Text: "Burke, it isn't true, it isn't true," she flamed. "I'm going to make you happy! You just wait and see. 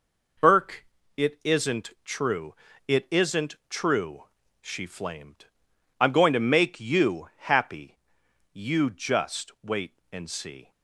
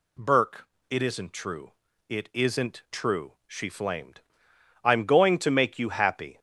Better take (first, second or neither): first